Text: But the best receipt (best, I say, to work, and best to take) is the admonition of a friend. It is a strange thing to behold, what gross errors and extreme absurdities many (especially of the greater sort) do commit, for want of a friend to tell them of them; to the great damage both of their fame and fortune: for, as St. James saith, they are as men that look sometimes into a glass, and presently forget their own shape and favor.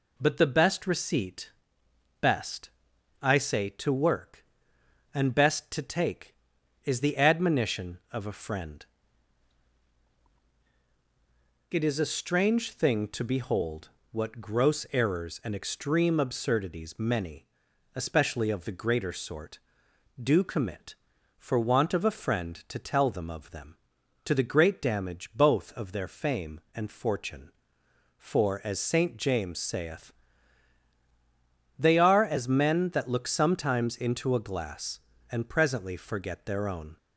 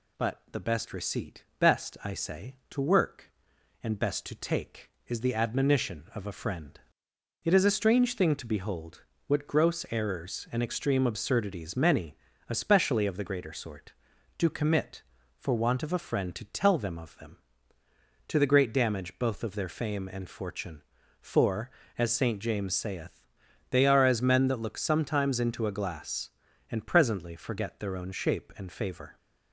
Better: second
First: stops before "shape and favor"; at 36.9 s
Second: none

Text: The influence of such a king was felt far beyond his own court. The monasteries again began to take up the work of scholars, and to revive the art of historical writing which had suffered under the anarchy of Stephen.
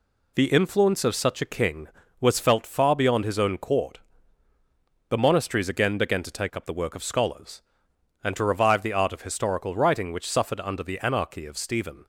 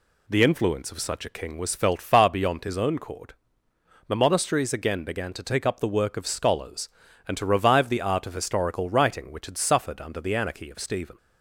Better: second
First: skips "had"; at 10.2 s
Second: none

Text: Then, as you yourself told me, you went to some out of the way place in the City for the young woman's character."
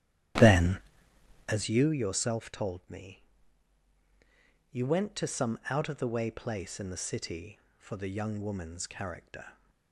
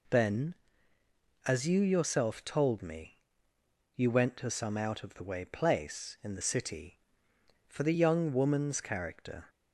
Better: second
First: starts louder than the rest; strong; until 1.7 s; 11.5 dB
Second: none

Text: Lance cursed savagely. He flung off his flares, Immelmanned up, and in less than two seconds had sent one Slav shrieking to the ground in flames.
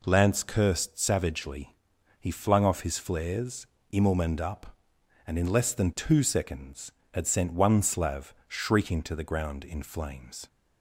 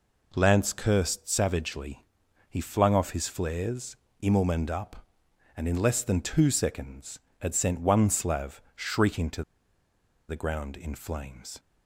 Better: first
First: none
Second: pauses between "to" and "the"; noticeable; at 9.4 s; 0.86 s long

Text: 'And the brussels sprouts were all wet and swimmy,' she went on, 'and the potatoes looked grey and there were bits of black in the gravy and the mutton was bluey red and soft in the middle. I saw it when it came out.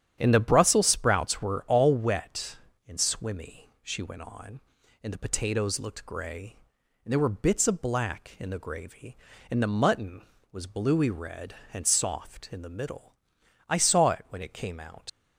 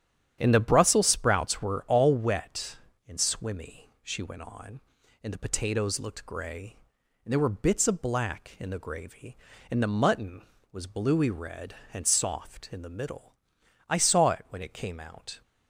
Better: second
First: starts louder than the rest; strong; until 1.1 s; 10 dB // leaves "out" unfinished; at 15.0 s; 115 ms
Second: starts louder than the rest; strong; until 1.4 s; 9.5 dB

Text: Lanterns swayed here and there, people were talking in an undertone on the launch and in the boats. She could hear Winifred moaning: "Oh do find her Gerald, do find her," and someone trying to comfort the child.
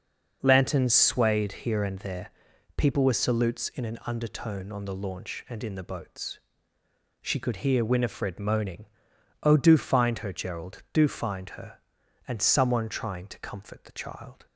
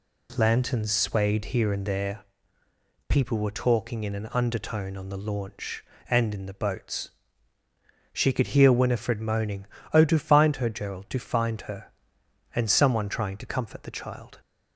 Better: second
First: starts louder than the rest; noticeable; until 1.4 s; 6 dB // says "salutes" for "talking"; at 3.1 s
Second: none

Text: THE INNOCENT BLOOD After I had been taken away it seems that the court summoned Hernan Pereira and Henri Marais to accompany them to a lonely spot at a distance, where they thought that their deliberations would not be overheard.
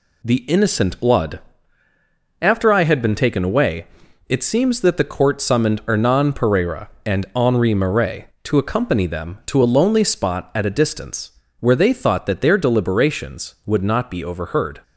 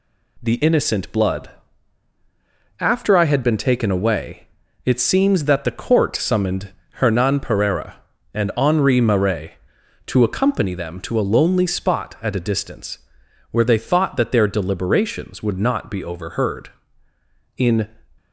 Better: first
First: pauses between "BLOOD" and "After"; at 1.4 s; 1.0 s long // pauses between "away" and "it"; at 3.8 s; 0.42 s long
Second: pauses between "BLOOD" and "After"; strong; at 1.4 s; 1.2 s long // pauses between "away" and "it"; at 4.4 s; 0.40 s long // pauses between "summoned" and "Hernan"; slight; at 6.7 s; 0.20 s long // goes on to say "In"; slight; from 17.5 s on; 0.32 s long

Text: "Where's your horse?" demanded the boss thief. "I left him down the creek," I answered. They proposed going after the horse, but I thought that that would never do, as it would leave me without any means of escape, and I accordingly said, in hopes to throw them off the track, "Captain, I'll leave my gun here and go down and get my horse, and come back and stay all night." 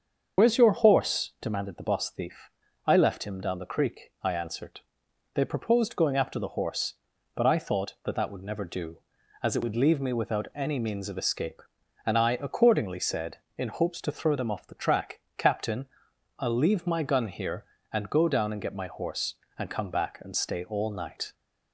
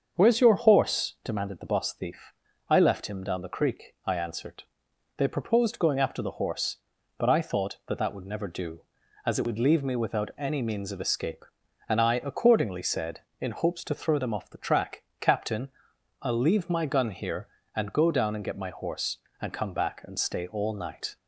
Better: second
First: loses the start of "Where's"; at 0.3 s; 40 ms // starts louder than the rest; until 1.4 s; 7 dB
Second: starts louder than the rest; until 1.2 s; 7 dB

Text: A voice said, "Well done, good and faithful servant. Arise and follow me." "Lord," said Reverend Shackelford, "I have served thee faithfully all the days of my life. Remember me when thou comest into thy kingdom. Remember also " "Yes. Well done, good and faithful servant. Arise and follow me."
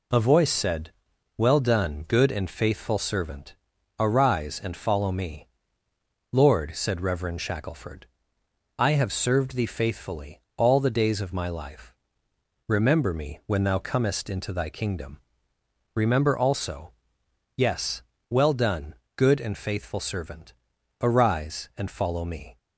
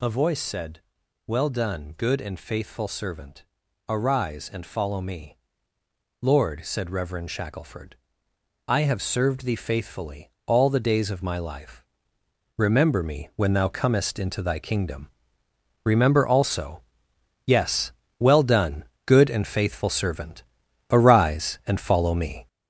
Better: first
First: pauses between "faithfully" and "all"; slight; at 10.4 s; 0.16 s long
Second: gets louder; throughout; 3.5 dB // pauses between "faithfully" and "all"; slight; at 10.3 s; 0.16 s long

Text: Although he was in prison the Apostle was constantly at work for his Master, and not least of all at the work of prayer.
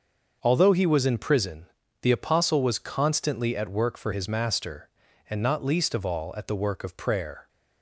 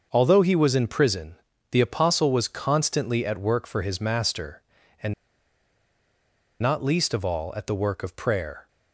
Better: first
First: starts louder than the rest; noticeable; until 1.4 s; 6 dB // pauses between "prison" and "the"; slight; at 1.6 s; 0.36 s long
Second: starts louder than the rest; noticeable; until 1.1 s; 6 dB // pauses between "prison" and "the"; slight; at 1.3 s; 0.36 s long // pauses between "and" and "not"; strong; at 5.1 s; 1.4 s long

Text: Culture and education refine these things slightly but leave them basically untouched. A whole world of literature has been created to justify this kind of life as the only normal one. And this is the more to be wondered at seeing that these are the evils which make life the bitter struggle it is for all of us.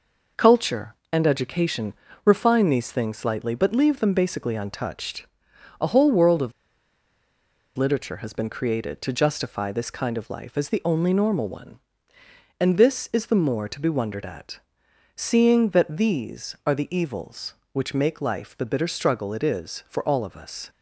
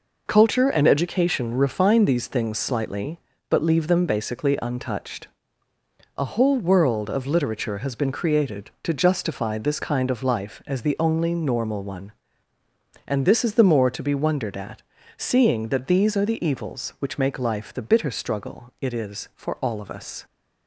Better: second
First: pauses between "education" and "refine"; slight; at 1.9 s; 0.32 s long // pauses between "of" and "literature"; strong; at 6.5 s; 1.2 s long // pauses between "at" and "seeing"; noticeable; at 14.5 s; 0.58 s long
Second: pauses between "at" and "seeing"; slight; at 14.8 s; 0.34 s long

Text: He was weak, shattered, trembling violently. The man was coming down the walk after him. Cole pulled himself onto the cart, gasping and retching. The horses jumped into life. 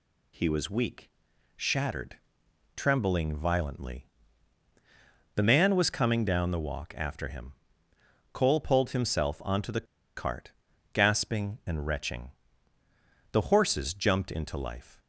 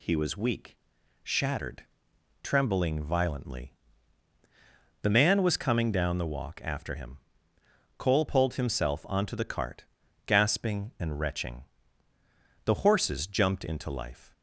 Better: second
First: pauses between "the" and "cart"; slight; at 9.8 s; 0.31 s long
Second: none

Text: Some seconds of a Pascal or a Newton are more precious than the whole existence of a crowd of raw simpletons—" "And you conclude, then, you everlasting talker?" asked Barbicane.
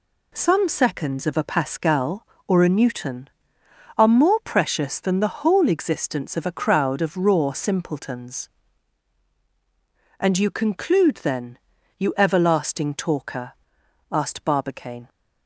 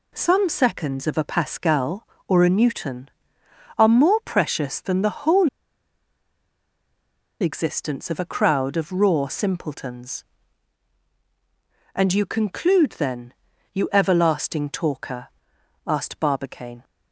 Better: first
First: none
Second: pauses between "whole" and "existence"; strong; at 5.4 s; 1.9 s long

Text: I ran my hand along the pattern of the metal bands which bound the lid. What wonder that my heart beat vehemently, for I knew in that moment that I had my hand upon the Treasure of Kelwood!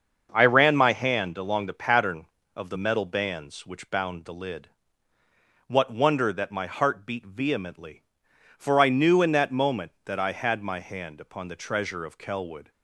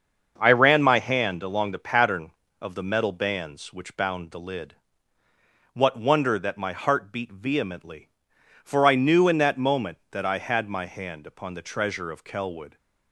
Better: neither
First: starts louder than the rest; until 1.3 s; 6.5 dB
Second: starts louder than the rest; until 1.3 s; 6.5 dB

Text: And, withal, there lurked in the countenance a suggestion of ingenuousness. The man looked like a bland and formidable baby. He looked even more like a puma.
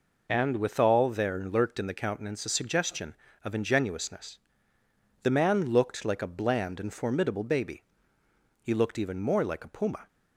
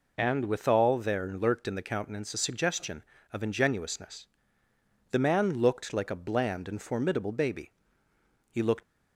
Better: first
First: none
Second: stops before "even more like a puma"; at 8.8 s

